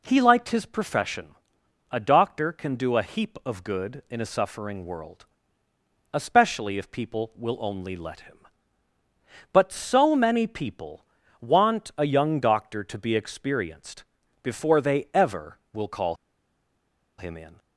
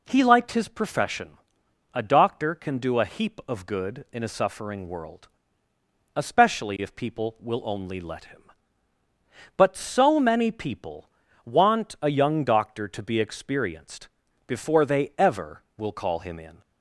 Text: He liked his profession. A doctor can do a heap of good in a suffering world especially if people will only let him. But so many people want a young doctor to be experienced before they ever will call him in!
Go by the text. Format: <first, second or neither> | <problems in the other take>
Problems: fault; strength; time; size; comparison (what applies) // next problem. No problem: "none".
second | pauses between "world" and "especially"; noticeable; at 5.2 s; 0.90 s long; noticeable in the second // pauses between "people" and "want"; slight; at 11.0 s; 0.34 s long; slight in the second // pauses between "experienced" and "before"; at 14.0 s; 0.38 s long; also in the second // pauses between "call" and "him"; at 16.1 s; 1.0 s long